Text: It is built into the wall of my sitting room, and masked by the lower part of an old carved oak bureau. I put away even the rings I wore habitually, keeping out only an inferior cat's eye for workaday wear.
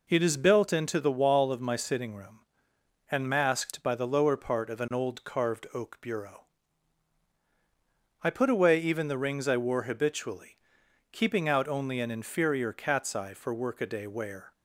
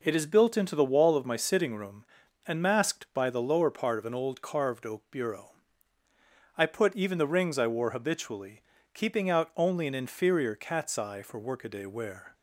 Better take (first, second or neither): first